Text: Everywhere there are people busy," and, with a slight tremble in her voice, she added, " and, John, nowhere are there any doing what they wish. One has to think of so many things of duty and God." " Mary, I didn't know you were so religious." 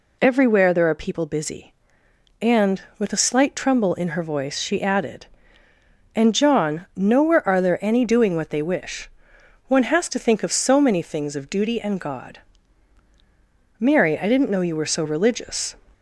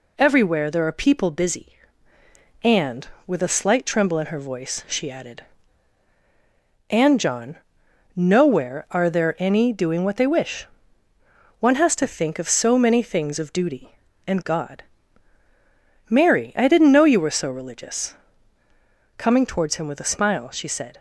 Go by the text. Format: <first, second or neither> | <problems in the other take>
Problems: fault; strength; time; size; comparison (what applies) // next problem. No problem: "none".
first | goes on to say "Coming towards him with a smile she said"; strong; from 19.1 s on; 1.8 s long